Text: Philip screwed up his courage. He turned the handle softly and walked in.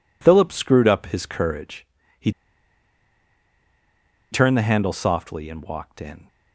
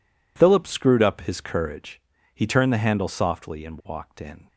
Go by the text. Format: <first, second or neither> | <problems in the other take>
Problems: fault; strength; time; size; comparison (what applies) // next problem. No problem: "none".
second | pauses between "He" and "turned"; strong; at 2.3 s; 2.0 s long